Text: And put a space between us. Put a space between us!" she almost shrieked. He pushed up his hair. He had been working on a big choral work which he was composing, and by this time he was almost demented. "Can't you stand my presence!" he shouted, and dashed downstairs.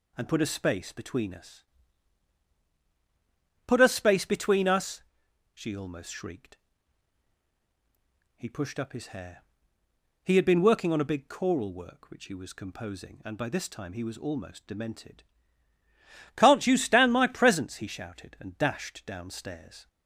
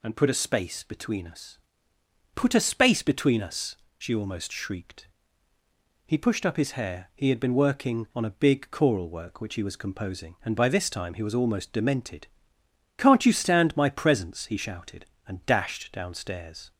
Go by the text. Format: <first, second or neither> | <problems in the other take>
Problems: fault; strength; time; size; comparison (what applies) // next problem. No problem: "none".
neither | none